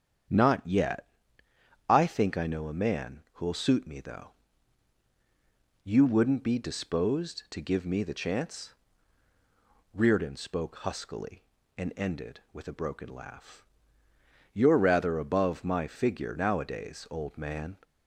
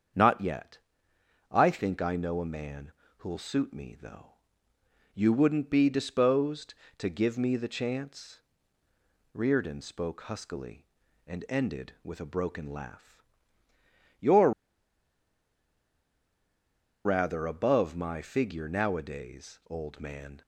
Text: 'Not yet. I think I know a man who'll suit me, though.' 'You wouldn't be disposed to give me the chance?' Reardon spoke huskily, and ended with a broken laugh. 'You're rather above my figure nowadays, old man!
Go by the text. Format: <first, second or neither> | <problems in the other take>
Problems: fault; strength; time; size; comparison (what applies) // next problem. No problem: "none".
first | starts louder than the rest; strong; until 1.9 s; 7.5 dB; strong in the first // pauses between "man" and "who'll"; slight; at 2.9 s; 0.26 s long // pauses between "You're" and "rather"; strong; at 14.5 s; 2.5 s long